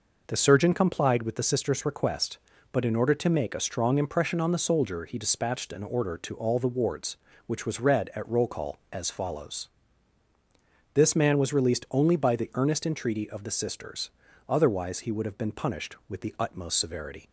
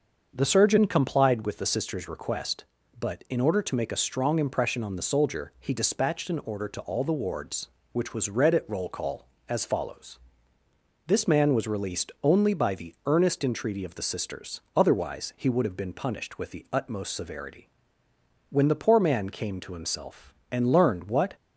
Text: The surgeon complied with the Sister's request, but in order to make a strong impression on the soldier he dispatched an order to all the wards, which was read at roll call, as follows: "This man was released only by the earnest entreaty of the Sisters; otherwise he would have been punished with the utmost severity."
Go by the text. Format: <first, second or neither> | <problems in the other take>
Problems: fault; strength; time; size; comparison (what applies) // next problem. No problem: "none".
first | starts louder than the rest; until 1.3 s; 6.5 dB // goes on to say "When the poor man came to himself and learned what"; strong; from 18.5 s on; 2.8 s long